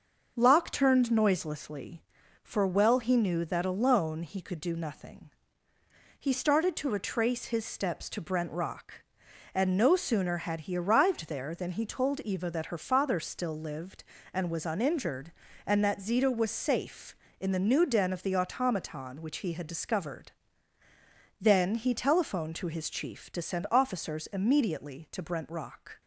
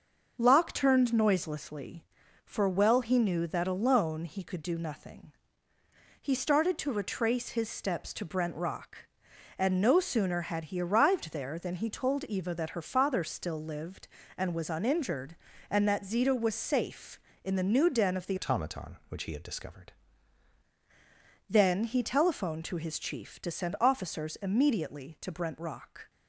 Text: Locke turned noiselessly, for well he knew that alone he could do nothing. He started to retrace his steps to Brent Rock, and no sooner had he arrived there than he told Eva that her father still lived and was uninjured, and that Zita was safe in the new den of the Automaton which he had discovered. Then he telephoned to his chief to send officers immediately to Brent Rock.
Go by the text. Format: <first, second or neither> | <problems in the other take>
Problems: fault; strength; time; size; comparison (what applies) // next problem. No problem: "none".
first | starts louder than the rest; until 1.3 s; 6.5 dB; also in the first // changes voice from "Automaton" to "discovered"; from 18.3 to 19.9 s; 1.6 s long